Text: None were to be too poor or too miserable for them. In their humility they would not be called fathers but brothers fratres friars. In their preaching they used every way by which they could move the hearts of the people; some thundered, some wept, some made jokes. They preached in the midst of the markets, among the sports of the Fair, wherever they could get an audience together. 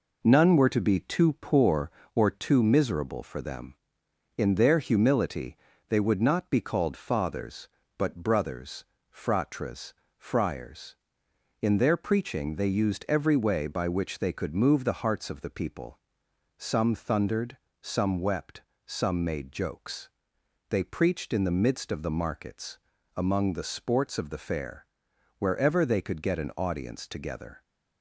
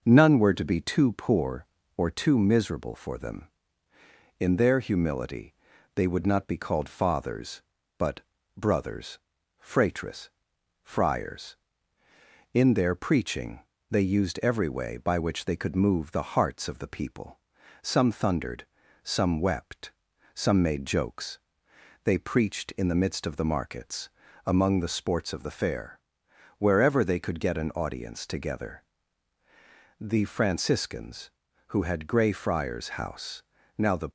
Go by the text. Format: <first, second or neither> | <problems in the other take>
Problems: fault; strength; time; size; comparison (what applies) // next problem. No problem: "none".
first | pauses between "humility" and "they"; at 5.5 s; 0.42 s long; slight in the first // pauses between "but" and "brothers"; slight; at 8.2 s; 0.36 s long // pauses between "brothers" and "fratres"; at 9.1 s; 0.42 s long; slight in the first // pauses between "fratres" and "friars"; noticeable; at 10.2 s; 0.54 s long; slight in the first // pauses between "preaching" and "they"; slight; at 13.6 s; 0.30 s long // goes on to say "The Franciscans who had Grey Friars House now the"; strong; from 29.9 s on; 4.1 s long